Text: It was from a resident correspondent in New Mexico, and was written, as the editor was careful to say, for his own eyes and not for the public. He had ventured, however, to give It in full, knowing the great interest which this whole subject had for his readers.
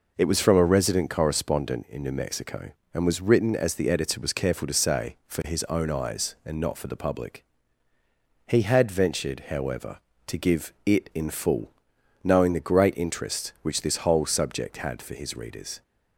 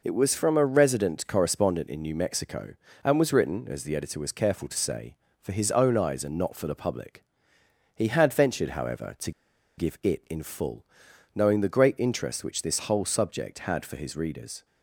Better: first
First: none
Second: pauses between "to" and "give"; at 9.3 s; 0.45 s long

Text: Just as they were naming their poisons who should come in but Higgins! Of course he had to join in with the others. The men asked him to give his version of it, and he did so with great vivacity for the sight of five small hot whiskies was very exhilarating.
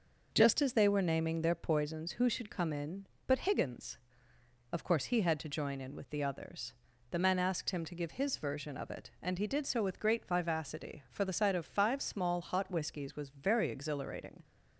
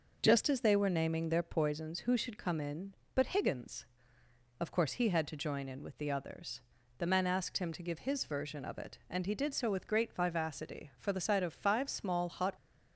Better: first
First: none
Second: stops before "whiskies was very exhilarating"; at 12.5 s

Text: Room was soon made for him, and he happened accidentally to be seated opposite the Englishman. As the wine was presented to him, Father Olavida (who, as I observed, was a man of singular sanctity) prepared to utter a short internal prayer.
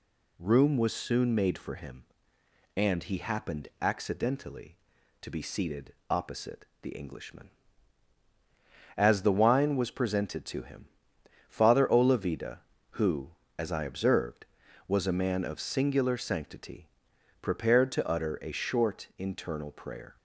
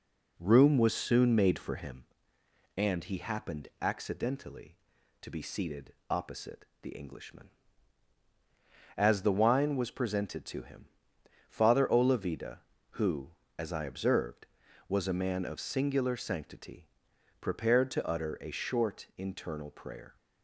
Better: first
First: pauses between "seated" and "opposite"; slight; at 5.9 s; 0.16 s long // pauses between "opposite" and "the"; slight; at 6.6 s; 0.16 s long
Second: starts louder than the rest; slight; until 2.1 s; 3 dB // pauses between "seated" and "opposite"; slight; at 5.9 s; 0.16 s long // pauses between "opposite" and "the"; slight; at 6.6 s; 0.16 s long

